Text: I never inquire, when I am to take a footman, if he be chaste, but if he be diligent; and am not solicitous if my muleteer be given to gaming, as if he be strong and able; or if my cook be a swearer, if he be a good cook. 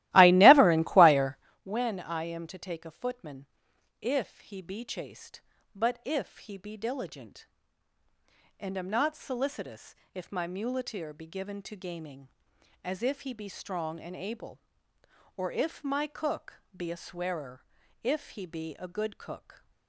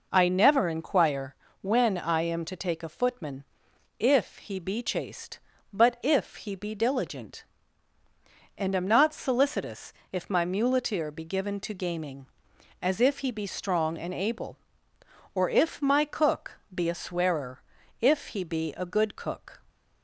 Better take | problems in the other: second | starts louder than the rest; strong; until 1.6 s; 16.5 dB // pauses between "solicitous" and "if"; slight; at 9.9 s; 0.18 s long; slight in the second // pauses between "cook" and "be"; slight; at 16.5 s; 0.16 s long; slight in the second

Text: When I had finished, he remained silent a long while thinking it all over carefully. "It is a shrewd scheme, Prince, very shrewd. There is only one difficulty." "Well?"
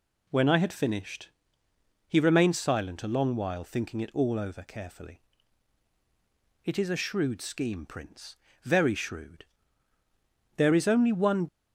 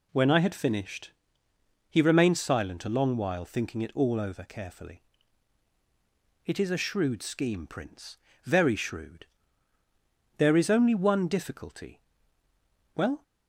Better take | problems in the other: second | stops before "difficulty Well"; at 11.4 s

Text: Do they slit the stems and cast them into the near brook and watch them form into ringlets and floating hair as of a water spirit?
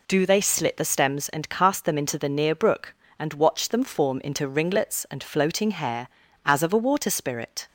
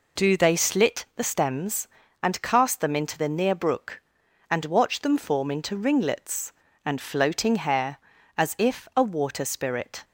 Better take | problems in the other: first | says "if" for "of"; at 8.5 s

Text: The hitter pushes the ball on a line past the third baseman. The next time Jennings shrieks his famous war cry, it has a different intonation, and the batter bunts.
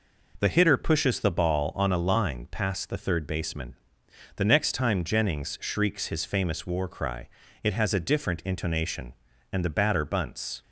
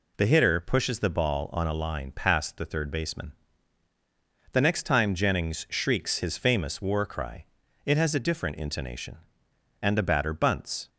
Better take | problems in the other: neither | none

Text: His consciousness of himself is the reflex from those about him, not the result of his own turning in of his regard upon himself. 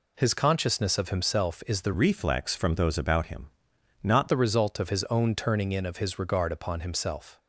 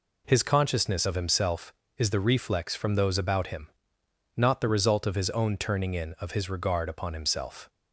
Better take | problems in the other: second | changes voice from "reflex" to "not"; from 1.9 to 4.2 s; 2.3 s long

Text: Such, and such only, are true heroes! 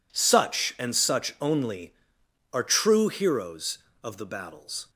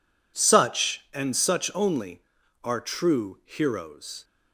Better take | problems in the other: second | goes on to say "Of the battles"; noticeable; from 4.0 s on; 0.88 s long

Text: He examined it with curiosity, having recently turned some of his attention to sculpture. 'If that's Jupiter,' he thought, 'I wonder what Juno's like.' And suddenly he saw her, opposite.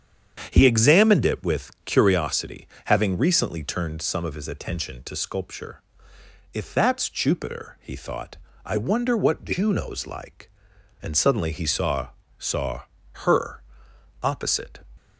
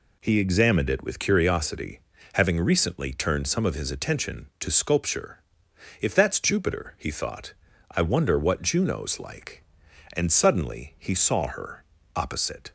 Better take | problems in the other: second | starts louder than the rest; strong; until 1.5 s; 8 dB // says "saw" twice; at 12.3 s

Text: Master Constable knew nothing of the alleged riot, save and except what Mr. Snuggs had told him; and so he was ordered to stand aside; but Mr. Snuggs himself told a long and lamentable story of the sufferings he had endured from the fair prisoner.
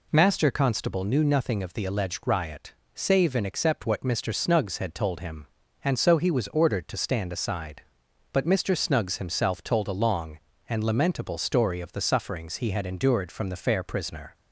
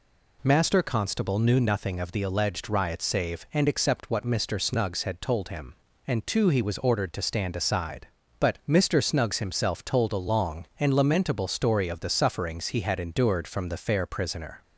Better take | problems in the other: first | says "too" for "so"; at 6.2 s

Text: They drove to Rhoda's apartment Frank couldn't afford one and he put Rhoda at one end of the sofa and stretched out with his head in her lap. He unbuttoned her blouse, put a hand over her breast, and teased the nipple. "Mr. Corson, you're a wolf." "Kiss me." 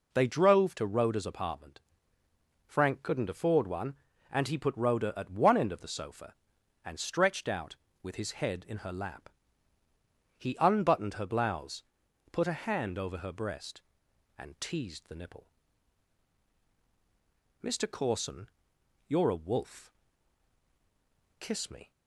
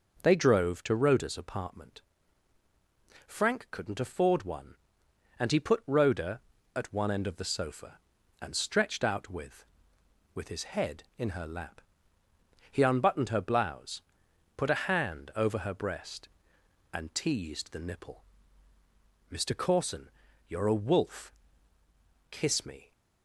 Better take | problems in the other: first | pauses between "apartment" and "Frank"; strong; at 2.0 s; 1.2 s long; noticeable in the first // says "with" twice; at 10.3 s

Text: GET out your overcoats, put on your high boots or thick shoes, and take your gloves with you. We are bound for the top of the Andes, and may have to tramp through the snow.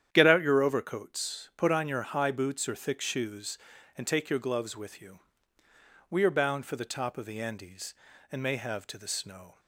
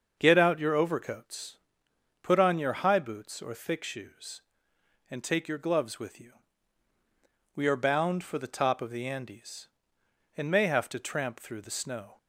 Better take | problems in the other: second | starts louder than the rest; strong; until 1.1 s; 10 dB; also in the second // skips "tramp through"; at 8.9 s

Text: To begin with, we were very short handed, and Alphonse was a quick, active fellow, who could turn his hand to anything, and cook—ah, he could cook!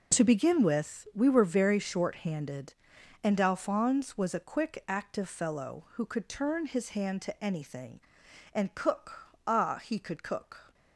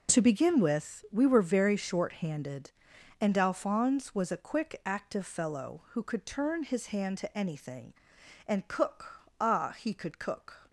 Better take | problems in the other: neither | none

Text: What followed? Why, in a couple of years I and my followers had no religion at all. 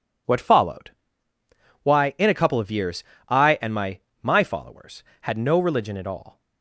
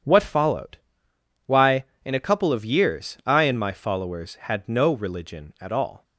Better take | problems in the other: second | pauses between "years" and "I"; slight; at 3.0 s; 0.26 s long // says "my" twice; at 4.2 s

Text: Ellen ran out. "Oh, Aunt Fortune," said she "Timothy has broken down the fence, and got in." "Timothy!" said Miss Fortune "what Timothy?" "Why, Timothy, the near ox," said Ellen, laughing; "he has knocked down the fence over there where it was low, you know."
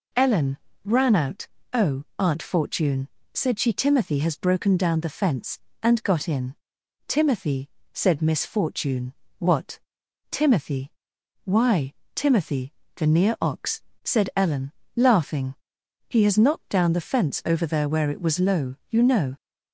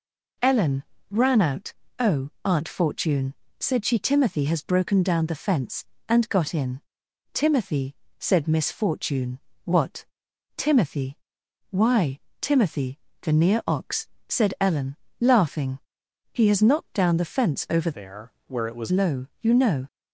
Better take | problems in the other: first | pauses between "Ellen" and "ran"; slight; at 0.8 s; 0.26 s long; slight in the first // pauses between "Fortune" and "what"; slight; at 9.3 s; 0.24 s long; slight in the first // pauses between "what" and "Timothy"; noticeable; at 10.0 s; 0.52 s long; noticeable in the first // changes voice from "there" to "was"; from 17.9 to 18.9 s; 1.0 s long // pauses between "there" and "where"; slight; at 18.3 s; 0.16 s long

